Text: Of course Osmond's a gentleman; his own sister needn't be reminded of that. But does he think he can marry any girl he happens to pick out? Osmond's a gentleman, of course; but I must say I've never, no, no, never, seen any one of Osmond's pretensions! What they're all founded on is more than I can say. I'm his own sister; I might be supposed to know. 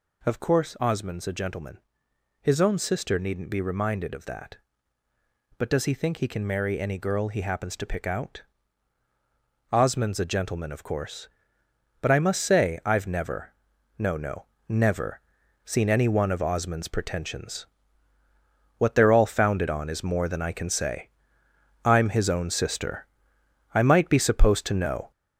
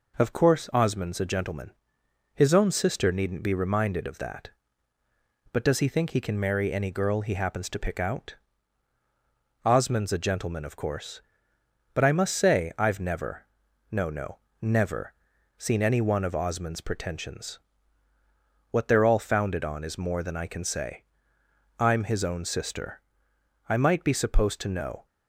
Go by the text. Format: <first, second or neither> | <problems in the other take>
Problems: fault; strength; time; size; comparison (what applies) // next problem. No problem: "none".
second | gets louder; noticeable; throughout; 5.5 dB